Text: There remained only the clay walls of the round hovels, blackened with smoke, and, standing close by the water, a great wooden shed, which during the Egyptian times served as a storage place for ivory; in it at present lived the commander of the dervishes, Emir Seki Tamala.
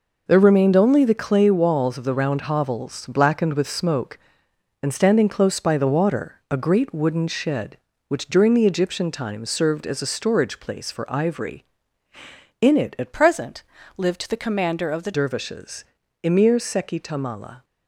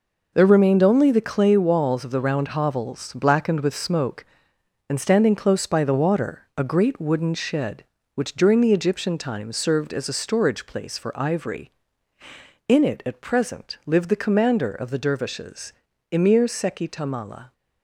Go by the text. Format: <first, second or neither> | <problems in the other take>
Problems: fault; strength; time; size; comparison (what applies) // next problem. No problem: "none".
second | changes voice from "present" to "the"; from 13.1 to 15.1 s; 2.0 s long // pauses between "present" and "lived"; slight; at 13.6 s; 0.34 s long